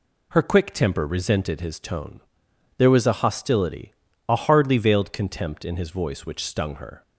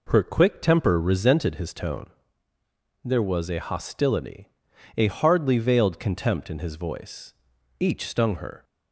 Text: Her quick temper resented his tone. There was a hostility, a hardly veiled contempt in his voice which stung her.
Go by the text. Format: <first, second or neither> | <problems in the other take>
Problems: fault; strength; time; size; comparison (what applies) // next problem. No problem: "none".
first | says "each" for "which"; at 7.7 s